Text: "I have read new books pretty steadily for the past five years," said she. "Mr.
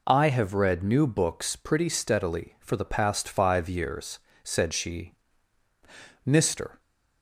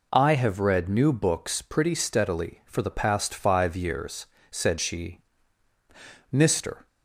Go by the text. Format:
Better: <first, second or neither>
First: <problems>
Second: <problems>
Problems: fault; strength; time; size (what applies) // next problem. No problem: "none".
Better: neither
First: none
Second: none